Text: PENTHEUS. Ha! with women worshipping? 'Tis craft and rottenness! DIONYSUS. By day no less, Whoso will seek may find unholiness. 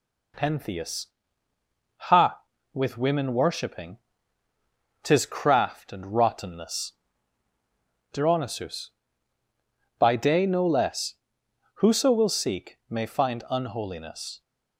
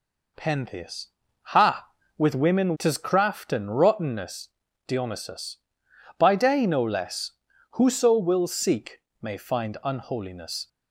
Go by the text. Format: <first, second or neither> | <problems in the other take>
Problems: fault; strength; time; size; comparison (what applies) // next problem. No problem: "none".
first | skips "worshipping"; at 2.7 s // pauses between "seek" and "may"; slight; at 8.9 s; 0.20 s long